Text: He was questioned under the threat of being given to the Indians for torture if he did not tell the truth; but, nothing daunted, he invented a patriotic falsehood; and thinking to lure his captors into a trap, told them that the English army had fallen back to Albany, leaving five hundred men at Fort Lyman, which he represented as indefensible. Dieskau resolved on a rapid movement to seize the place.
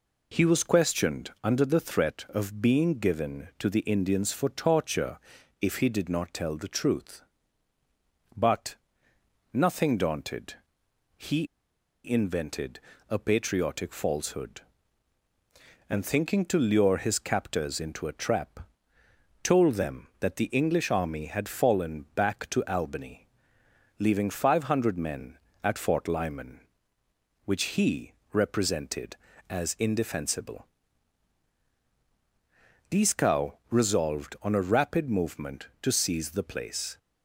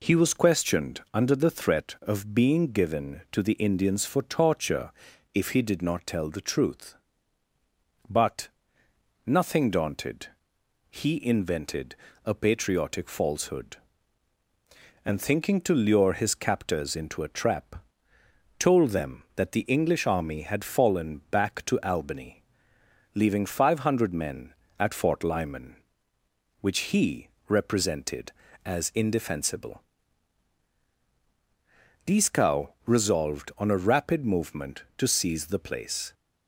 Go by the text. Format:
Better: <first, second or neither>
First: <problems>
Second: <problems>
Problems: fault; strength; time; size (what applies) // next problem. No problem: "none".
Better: second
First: pauses between "torture" and "if"; at 5.1 s; 0.42 s long // pauses between "he" and "invented"; noticeable; at 11.4 s; 0.59 s long // pauses between "invented" and "a"; slight; at 12.7 s; 0.28 s long // pauses between "he" and "represented"; slight; at 28.1 s; 0.20 s long // pauses between "Dieskau" and "resolved"; slight; at 33.5 s; 0.18 s long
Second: pauses between "torture" and "if"; at 4.9 s; 0.42 s long // pauses between "invented" and "a"; slight; at 11.9 s; 0.28 s long // pauses between "he" and "represented"; slight; at 27.2 s; 0.20 s long // pauses between "Dieskau" and "resolved"; slight; at 32.6 s; 0.18 s long